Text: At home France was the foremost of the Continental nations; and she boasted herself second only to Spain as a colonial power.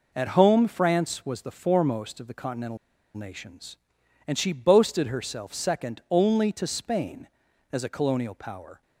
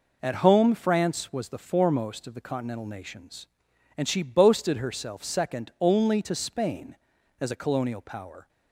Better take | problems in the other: second | pauses between "Continental" and "nations"; at 2.7 s; 0.37 s long

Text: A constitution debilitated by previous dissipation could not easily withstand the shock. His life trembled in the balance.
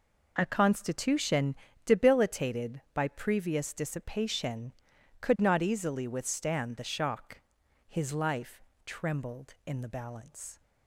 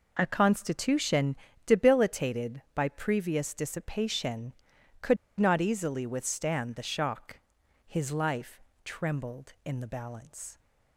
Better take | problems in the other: first | pauses between "constitution" and "debilitated"; slight; at 1.3 s; 0.32 s long; slight in the first // pauses between "could" and "not"; slight; at 5.1 s; 0.23 s long // pauses between "life" and "trembled"; slight; at 8.6 s; 0.24 s long; slight in the first

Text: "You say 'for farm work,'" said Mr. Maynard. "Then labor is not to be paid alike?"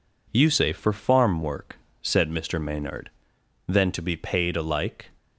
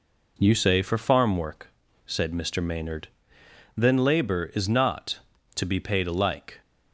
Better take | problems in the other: second | skips "labor is not"; at 3.9 s

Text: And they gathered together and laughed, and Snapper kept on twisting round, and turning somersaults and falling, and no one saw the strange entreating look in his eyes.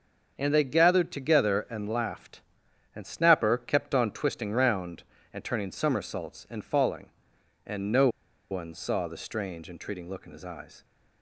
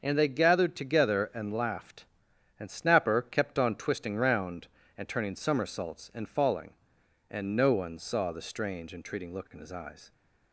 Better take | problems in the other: second | starts louder than the rest; until 1.3 s; 6.5 dB; also in the second // pauses between "no" and "one"; at 8.0 s; 0.42 s long

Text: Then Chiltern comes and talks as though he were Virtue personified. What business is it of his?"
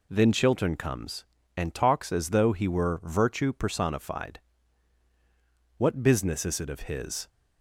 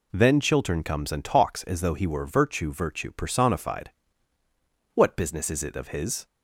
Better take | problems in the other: first | says "Virtue" twice; at 2.7 s

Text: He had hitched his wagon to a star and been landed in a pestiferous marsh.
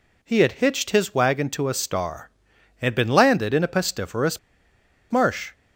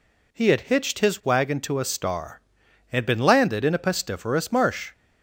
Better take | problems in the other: second | pauses between "pestiferous" and "marsh"; noticeable; at 4.3 s; 0.71 s long

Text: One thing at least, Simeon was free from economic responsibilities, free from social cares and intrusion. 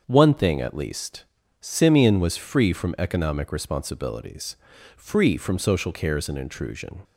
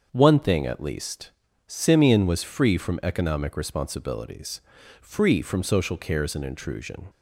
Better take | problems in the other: neither | starts louder than the rest; the same in both

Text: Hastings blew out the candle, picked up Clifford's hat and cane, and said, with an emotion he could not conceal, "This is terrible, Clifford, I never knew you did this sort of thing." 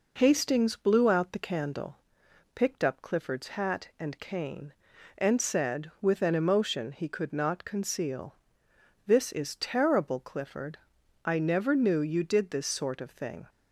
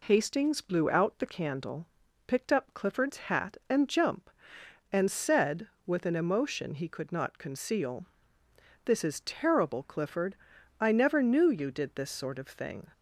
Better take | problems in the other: first | says "jump" for "cane"; at 3.8 s

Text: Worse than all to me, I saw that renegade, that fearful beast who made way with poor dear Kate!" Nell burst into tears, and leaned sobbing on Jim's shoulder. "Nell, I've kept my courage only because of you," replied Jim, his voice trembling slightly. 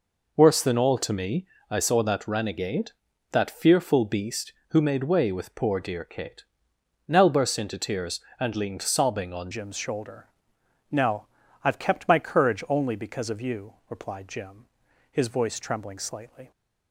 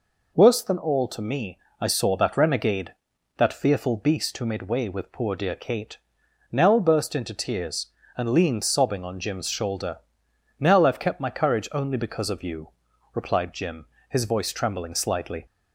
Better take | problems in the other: second | changes voice at "Jim's"; from 9.5 s on; 7.0 s long

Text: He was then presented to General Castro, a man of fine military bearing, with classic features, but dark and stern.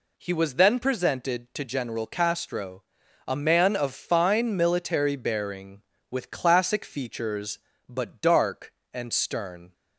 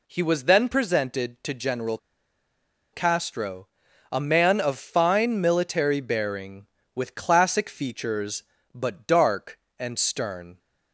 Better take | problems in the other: first | pauses between "General" and "Castro"; noticeable; at 1.9 s; 0.96 s long

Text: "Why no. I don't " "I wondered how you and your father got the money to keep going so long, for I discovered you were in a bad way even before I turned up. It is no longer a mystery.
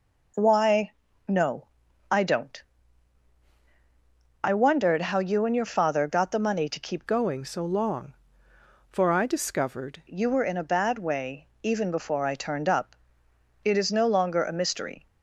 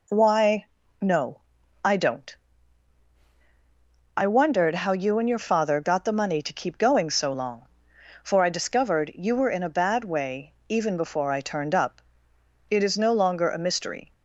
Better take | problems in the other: second | pauses between "Why" and "no"; at 0.8 s; 0.38 s long; also in the second // changes voice from "going" to "discovered"; from 7.0 to 10.0 s; 3.0 s long // pauses between "way" and "even"; slight; at 11.4 s; 0.16 s long; slight in the second

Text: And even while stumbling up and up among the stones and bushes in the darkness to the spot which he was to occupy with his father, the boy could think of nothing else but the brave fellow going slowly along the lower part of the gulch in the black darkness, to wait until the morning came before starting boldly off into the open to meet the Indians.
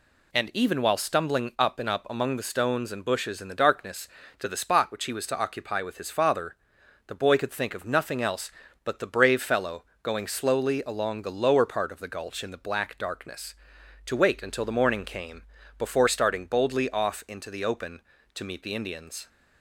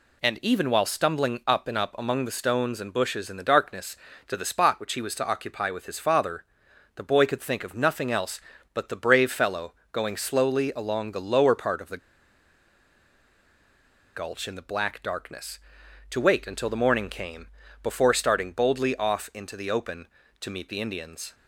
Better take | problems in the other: first | pauses between "fellow" and "going"; slight; at 9.7 s; 0.18 s long; slight in the first // pauses between "the" and "gulch"; strong; at 11.9 s; 2.1 s long // pauses between "came" and "before"; slight; at 17.4 s; 0.34 s long; slight in the first

